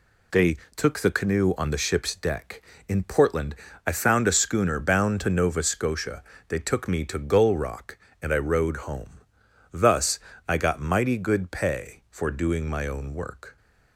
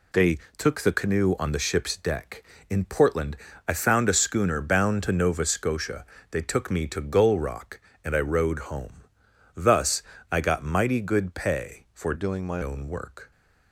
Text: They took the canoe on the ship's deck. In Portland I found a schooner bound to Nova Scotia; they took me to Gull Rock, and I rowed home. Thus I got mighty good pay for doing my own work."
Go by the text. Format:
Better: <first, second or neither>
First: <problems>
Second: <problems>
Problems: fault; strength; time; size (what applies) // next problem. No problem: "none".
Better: first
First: pauses between "They" and "took"; slight; at 0.5 s; 0.20 s long // pauses between "Portland" and "I"; slight; at 3.5 s; 0.32 s long // pauses between "Thus" and "I"; slight; at 10.1 s; 0.28 s long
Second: pauses between "They" and "took"; slight; at 0.3 s; 0.20 s long // pauses between "Portland" and "I"; slight; at 3.3 s; 0.32 s long // pauses between "Thus" and "I"; slight; at 10.0 s; 0.28 s long // changes voice from "doing" to "my"; from 12.1 to 12.6 s; 0.5 s long